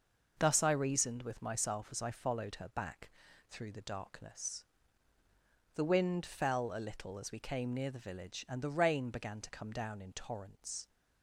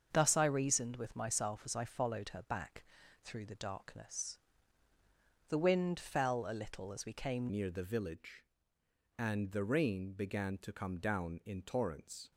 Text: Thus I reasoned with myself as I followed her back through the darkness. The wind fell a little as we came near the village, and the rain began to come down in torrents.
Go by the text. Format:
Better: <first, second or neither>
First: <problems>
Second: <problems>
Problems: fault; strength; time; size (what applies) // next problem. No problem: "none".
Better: first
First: pauses between "back" and "through"; at 3.0 s; 0.40 s long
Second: starts louder than the rest; until 1.1 s; 6.5 dB // pauses between "back" and "through"; at 2.8 s; 0.40 s long // changes voice at "near"; from 7.5 s on; 4.8 s long